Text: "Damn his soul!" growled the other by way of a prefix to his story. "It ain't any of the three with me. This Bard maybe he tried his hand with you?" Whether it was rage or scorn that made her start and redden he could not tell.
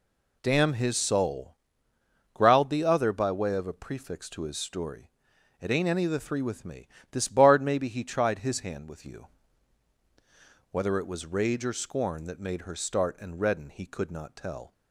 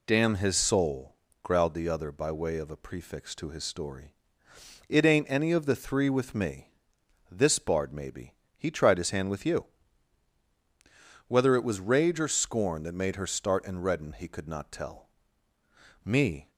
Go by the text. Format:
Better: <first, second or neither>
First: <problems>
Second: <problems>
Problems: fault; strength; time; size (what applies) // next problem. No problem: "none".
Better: first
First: none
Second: pauses between "maybe" and "he"; slight; at 8.3 s; 0.24 s long // goes on to say "Me"; slight; from 16.0 s on; 0.46 s long